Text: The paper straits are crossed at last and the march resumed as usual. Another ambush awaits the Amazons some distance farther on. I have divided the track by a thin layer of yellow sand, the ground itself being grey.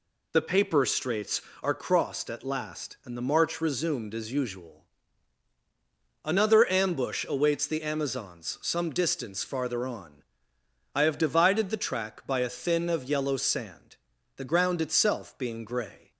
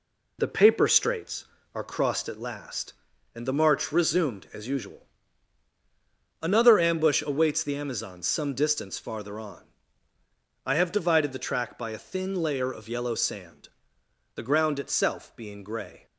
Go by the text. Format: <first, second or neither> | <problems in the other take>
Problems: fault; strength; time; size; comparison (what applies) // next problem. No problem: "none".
second | skips "layer"; at 12.8 s